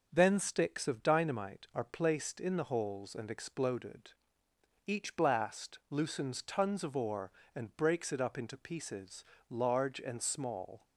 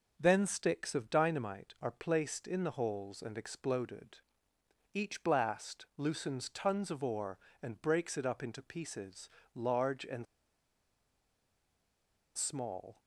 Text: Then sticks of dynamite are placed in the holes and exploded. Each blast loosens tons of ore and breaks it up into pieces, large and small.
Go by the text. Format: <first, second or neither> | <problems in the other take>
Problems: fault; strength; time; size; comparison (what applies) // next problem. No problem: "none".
first | starts louder than the rest; noticeable; until 1.1 s; 6 dB; noticeable in the first // pauses between "and" and "small"; strong; at 10.2 s; 2.1 s long